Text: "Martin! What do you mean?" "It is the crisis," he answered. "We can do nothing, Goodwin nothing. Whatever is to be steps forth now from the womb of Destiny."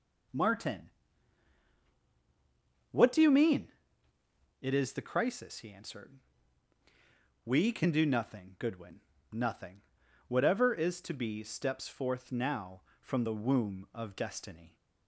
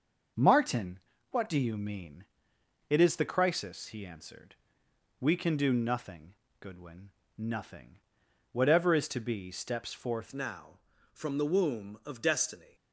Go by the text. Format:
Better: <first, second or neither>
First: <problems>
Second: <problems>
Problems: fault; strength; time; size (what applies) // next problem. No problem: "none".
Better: first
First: pauses between "Goodwin" and "nothing"; slight; at 9.0 s; 0.32 s long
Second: starts louder than the rest; until 1.6 s; 6.5 dB // pauses between "Goodwin" and "nothing"; slight; at 7.1 s; 0.26 s long // changes voice at "now"; from 10.3 s on; 2.4 s long